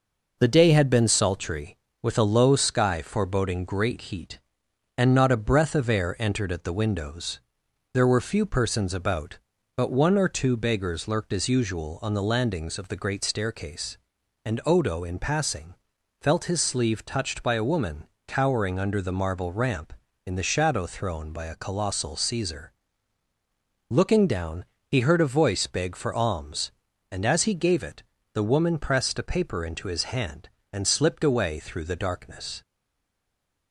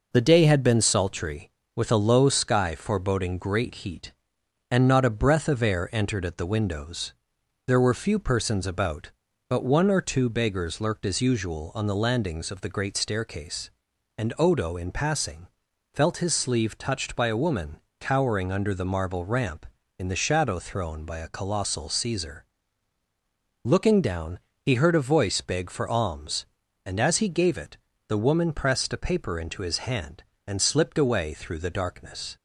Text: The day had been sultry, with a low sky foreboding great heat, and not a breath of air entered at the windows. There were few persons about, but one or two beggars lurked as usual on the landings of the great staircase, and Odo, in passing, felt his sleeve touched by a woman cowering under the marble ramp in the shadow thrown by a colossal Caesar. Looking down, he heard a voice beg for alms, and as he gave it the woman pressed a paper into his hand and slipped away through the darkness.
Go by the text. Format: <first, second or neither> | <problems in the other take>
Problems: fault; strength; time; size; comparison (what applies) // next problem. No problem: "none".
second | pauses between "woman" and "cowering"; slight; at 18.0 s; 0.20 s long; slight in the second // pauses between "it" and "the"; slight; at 28.0 s; 0.30 s long; slight in the second // stays silent after the last word; from 32.6 s on; 1.1 s long